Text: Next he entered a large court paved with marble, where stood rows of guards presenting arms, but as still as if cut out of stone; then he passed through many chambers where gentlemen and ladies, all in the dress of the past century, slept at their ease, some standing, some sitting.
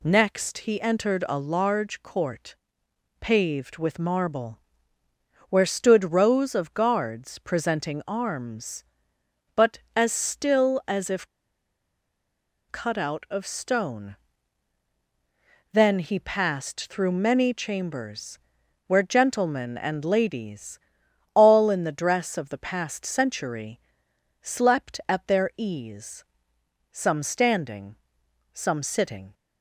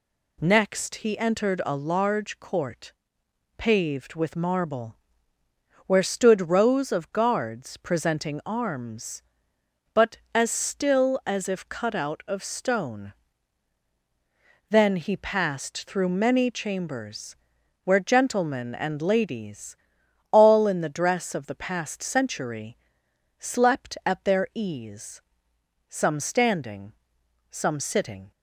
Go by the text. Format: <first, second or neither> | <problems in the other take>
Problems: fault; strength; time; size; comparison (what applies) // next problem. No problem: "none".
second | pauses between "court" and "paved"; noticeable; at 2.5 s; 0.64 s long; noticeable in the second // pauses between "if" and "cut"; strong; at 11.2 s; 1.4 s long // pauses between "chambers" and "where"; noticeable; at 18.3 s; 0.48 s long; noticeable in the second